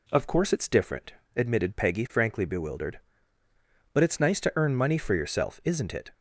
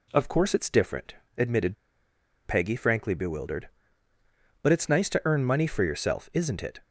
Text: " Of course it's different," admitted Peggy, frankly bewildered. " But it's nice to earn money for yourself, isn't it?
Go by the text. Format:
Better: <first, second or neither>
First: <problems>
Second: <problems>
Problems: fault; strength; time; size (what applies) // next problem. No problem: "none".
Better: first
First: none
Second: pauses between "admitted" and "Peggy"; noticeable; at 1.7 s; 0.70 s long